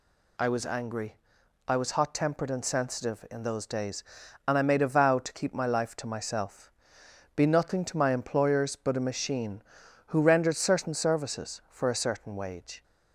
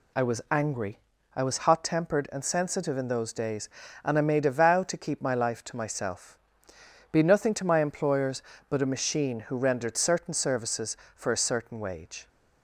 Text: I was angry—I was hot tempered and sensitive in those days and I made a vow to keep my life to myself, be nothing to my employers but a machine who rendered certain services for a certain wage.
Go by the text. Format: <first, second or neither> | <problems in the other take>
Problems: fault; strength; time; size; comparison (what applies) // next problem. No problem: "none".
neither | none